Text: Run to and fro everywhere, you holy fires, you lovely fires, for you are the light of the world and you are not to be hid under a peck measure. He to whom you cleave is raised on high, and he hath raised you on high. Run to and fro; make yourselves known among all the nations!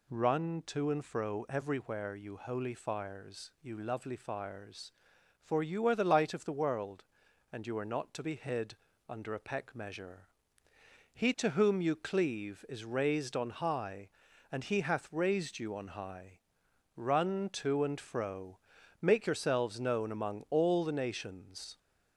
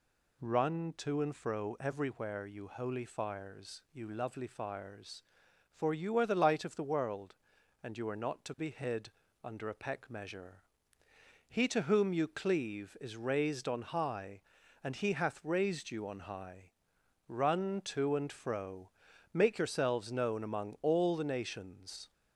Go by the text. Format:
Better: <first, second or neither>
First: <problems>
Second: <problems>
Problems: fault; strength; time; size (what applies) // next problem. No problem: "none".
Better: neither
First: pauses between "hid" and "under"; slight; at 8.7 s; 0.32 s long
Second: pauses between "hid" and "under"; slight; at 9.0 s; 0.32 s long